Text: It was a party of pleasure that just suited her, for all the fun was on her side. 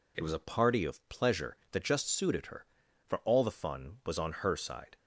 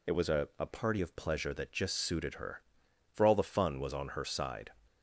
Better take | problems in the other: first | says "a" twice; at 0.5 s

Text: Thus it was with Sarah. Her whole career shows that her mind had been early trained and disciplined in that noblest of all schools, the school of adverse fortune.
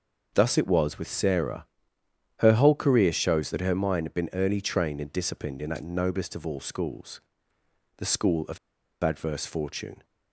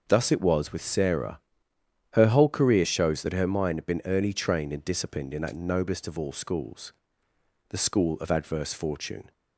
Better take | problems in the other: second | starts louder than the rest; until 1.3 s; 6 dB; noticeable in the second // pauses between "of" and "adverse"; noticeable; at 8.5 s; 0.46 s long

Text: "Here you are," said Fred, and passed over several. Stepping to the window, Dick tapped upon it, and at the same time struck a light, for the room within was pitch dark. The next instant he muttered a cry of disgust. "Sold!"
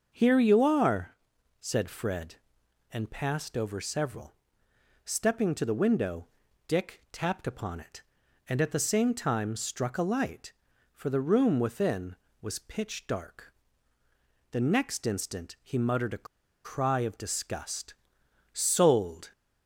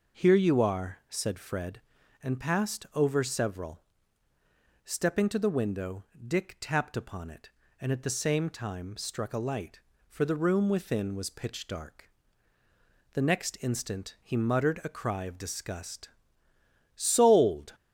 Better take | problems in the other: second | starts louder than the rest; until 1.1 s; 6.5 dB // pauses between "a" and "cry"; at 16.2 s; 0.38 s long

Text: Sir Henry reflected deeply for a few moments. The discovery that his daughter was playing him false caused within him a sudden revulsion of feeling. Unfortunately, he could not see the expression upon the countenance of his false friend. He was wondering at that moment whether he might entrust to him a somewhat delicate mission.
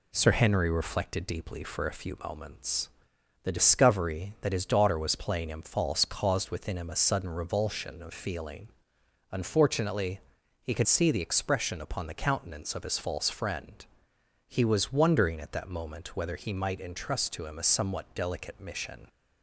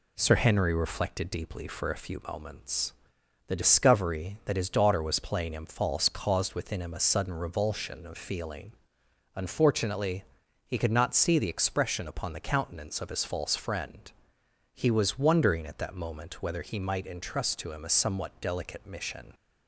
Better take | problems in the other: second | skips "not"; at 10.8 s

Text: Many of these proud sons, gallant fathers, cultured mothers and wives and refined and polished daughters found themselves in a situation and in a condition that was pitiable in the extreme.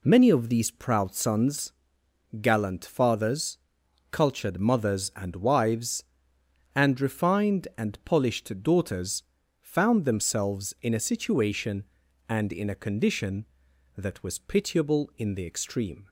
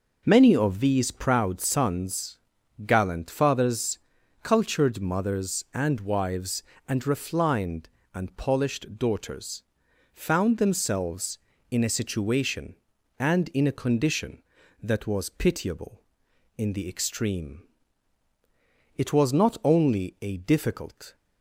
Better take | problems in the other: first | pauses between "daughters" and "found"; noticeable; at 9.6 s; 0.50 s long; also in the first // goes on to say "It was not only a difficult"; strong; from 18.9 s on; 2.2 s long

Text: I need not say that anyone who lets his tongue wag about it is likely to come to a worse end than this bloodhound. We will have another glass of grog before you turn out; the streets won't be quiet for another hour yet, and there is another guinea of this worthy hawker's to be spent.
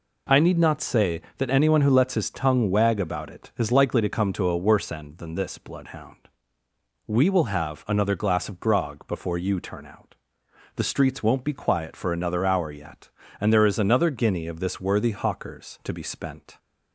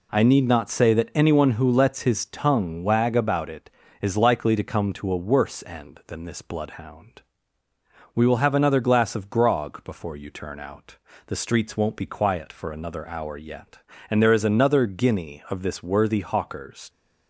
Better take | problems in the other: first | stops before "to be spent"; at 16.8 s

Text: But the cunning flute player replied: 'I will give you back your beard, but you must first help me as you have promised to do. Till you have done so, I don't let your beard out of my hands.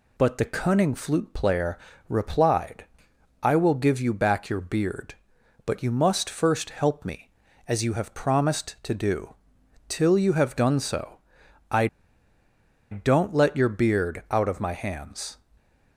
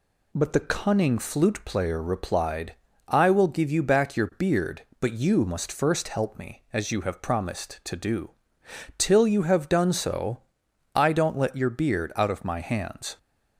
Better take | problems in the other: second | pauses between "player" and "replied"; slight; at 1.7 s; 0.32 s long // pauses between "I" and "don't"; at 11.8 s; 1.0 s long

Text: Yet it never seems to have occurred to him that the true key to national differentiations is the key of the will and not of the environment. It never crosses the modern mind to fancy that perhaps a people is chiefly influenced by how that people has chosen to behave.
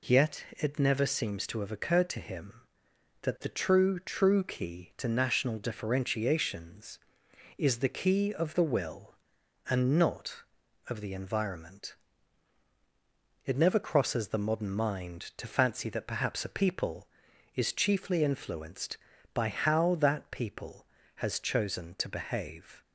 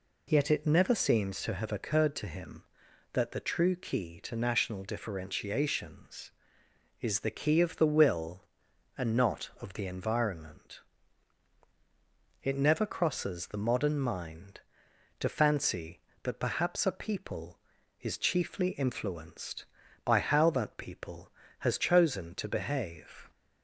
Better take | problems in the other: second | says "true" twice; at 3.9 s

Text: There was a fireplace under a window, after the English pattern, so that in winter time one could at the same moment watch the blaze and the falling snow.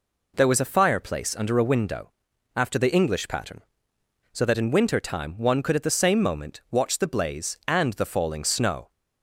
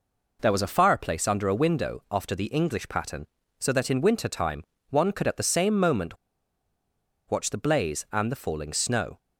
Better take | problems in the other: first | pauses between "time" and "one"; slight; at 4.6 s; 0.26 s long // pauses between "moment" and "watch"; at 6.1 s; 1.1 s long

